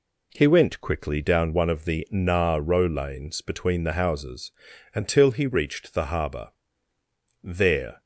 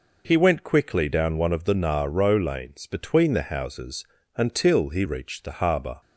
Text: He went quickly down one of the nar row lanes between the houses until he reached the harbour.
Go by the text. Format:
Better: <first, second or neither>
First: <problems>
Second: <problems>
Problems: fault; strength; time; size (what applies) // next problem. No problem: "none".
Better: second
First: pauses between "houses" and "until"; at 4.5 s; 0.44 s long // goes on to say "There"; from 7.4 s on; 0.58 s long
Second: pauses between "houses" and "until"; slight; at 4.0 s; 0.32 s long